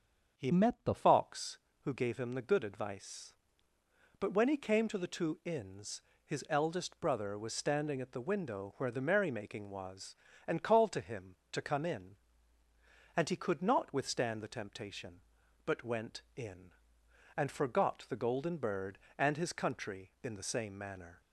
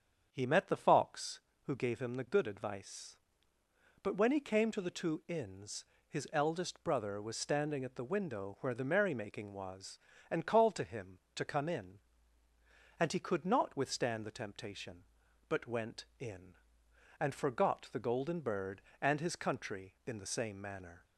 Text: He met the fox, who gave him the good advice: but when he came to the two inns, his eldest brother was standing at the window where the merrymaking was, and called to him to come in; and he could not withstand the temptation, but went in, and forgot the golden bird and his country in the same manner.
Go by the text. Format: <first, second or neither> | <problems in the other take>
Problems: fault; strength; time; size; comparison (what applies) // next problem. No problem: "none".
second | starts louder than the rest; until 1.4 s; 7 dB; strong in the second // changes voice from "met" to "the"; from 0.5 to 0.9 s; 0.4 s long